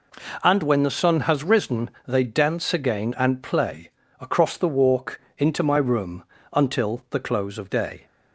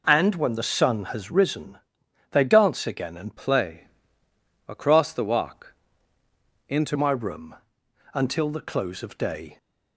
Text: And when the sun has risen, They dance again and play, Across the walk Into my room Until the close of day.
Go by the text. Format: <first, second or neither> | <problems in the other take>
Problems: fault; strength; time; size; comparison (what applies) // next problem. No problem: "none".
first | changes voice from "play" to "Into"; from 3.3 to 6.9 s; 3.6 s long // pauses between "walk" and "Into"; noticeable; at 5.7 s; 0.96 s long; slight in the first // pauses between "room" and "Until"; noticeable; at 7.5 s; 0.58 s long; slight in the first